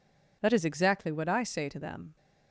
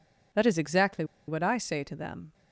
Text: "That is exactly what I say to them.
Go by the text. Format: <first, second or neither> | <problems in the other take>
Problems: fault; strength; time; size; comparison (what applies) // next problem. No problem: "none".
first | pauses between "exactly" and "what"; slight; at 1.0 s; 0.23 s long